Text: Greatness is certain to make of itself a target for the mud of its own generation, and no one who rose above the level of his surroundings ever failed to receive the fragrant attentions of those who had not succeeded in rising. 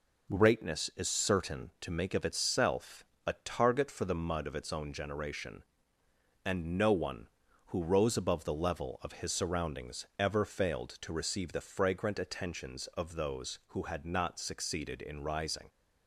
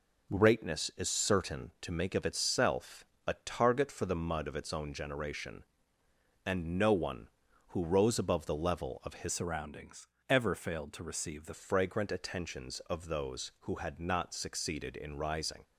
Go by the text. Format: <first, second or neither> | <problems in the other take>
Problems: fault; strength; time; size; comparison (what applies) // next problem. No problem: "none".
first | pauses between "itself" and "a"; slight; at 3.0 s; 0.20 s long; slight in the first // changes voice from "surroundings" to "the"; from 9.3 to 11.5 s; 2.2 s long // pauses between "surroundings" and "ever"; slight; at 10.0 s; 0.22 s long